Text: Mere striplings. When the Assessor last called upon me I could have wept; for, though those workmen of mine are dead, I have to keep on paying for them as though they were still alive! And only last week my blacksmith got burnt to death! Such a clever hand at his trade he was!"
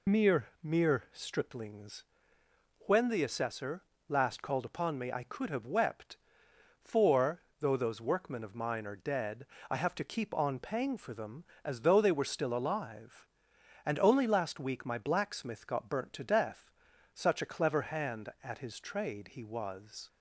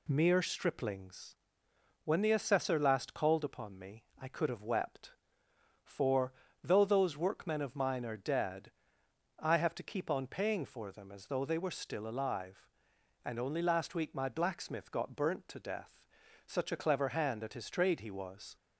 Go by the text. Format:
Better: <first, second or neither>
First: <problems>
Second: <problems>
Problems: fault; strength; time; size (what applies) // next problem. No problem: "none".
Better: second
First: says "Mere" twice; at 0.6 s // pauses between "Assessor" and "last"; slight; at 3.8 s; 0.26 s long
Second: none